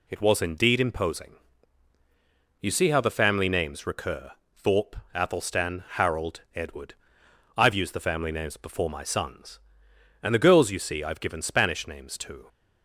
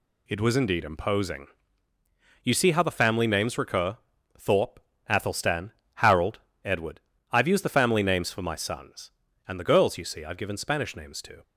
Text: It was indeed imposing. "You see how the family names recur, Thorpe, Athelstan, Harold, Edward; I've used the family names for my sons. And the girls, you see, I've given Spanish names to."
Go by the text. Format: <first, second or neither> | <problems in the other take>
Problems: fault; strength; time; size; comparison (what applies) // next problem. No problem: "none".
second | says "before" for "for"; at 8.5 s